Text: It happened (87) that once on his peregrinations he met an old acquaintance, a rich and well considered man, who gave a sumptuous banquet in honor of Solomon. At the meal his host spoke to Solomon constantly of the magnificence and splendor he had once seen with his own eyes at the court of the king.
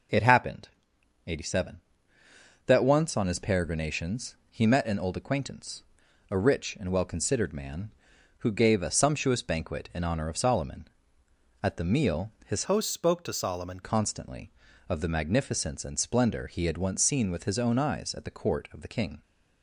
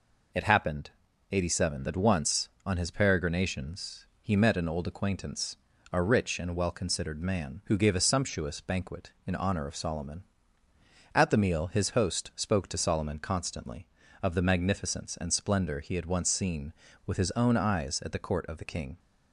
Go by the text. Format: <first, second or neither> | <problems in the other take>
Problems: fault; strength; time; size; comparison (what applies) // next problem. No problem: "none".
second | pauses between "peregrinations" and "he"; slight; at 4.3 s; 0.16 s long; slight in the second // changes voice from "host" to "Solomon"; from 12.6 to 13.8 s; 1.2 s long